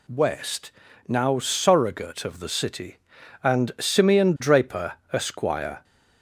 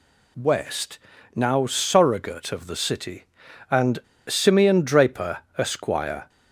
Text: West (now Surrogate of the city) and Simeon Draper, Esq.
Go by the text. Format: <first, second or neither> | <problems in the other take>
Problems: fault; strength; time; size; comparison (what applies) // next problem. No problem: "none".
first | pauses between "and" and "Simeon"; slight; at 3.9 s; 0.29 s long